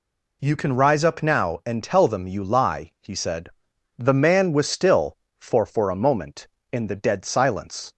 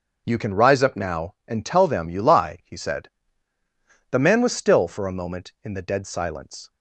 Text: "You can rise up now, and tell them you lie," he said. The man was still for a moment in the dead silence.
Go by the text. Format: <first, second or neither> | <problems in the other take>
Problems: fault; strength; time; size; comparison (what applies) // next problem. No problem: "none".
second | says "for" twice; at 5.6 s